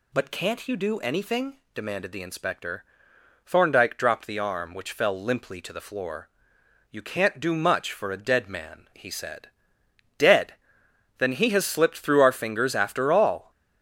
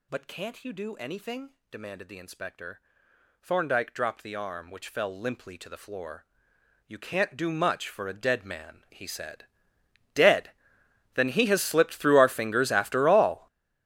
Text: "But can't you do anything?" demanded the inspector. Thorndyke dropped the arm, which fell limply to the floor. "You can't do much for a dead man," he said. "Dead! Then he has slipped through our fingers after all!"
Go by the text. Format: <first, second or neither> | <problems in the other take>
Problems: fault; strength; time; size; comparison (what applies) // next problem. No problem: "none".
first | gets louder; strong; throughout; 15 dB